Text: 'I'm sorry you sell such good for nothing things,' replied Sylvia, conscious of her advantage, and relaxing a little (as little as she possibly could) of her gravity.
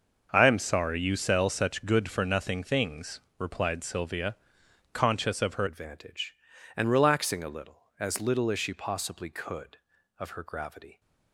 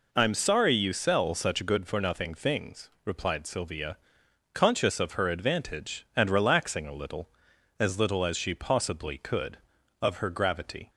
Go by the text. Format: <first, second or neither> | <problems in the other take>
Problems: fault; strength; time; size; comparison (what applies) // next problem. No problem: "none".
second | starts louder than the rest; noticeable; until 1.3 s; 6 dB // changes voice at "advantage"; from 5.6 s on; 5.4 s long